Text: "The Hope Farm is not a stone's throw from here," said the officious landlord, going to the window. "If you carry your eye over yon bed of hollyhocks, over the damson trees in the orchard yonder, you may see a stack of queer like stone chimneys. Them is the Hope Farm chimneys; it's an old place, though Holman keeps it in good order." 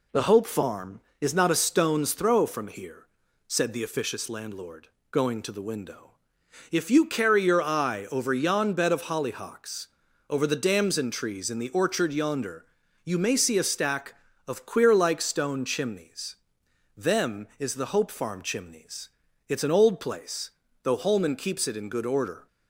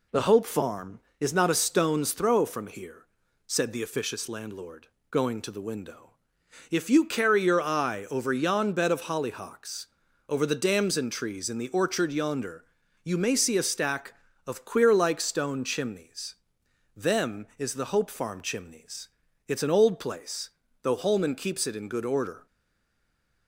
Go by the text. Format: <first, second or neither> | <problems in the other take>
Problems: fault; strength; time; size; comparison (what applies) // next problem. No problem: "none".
first | stays silent after the last word; from 22.4 s on; 1.0 s long